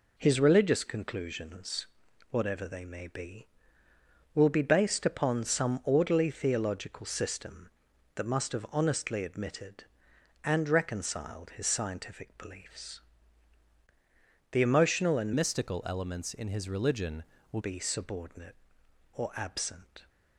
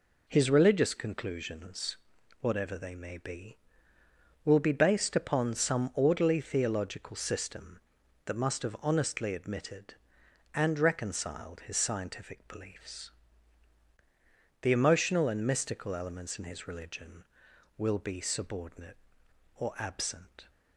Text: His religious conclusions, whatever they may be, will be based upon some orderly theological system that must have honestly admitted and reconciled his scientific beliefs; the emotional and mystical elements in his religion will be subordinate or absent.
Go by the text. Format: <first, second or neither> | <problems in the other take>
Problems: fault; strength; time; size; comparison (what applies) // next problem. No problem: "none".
second | changes voice from "mystical" to "will"; from 15.3 to 17.5 s; 2.2 s long